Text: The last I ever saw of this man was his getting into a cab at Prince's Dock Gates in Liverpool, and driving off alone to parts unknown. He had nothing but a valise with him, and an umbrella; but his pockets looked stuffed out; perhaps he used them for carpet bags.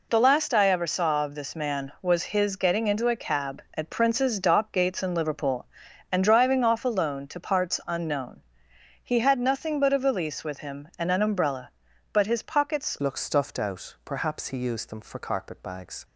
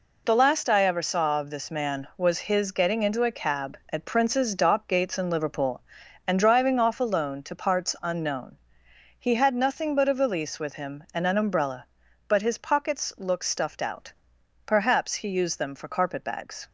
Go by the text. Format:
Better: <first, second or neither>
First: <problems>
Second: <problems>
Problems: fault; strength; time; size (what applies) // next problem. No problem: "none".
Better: second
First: changes voice at "looked"; from 12.9 s on; 3.1 s long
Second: none